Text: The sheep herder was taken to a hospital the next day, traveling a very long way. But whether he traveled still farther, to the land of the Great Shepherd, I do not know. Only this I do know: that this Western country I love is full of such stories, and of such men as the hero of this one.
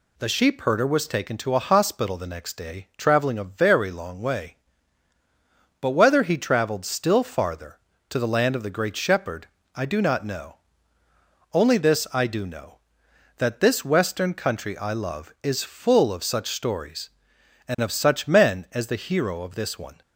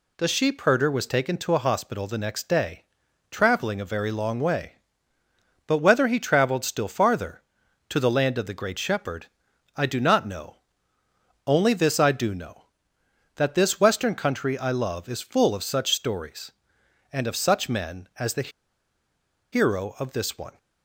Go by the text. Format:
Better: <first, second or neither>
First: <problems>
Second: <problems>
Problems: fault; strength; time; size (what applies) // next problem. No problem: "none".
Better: first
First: none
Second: pauses between "the" and "hero"; at 18.4 s; 1.0 s long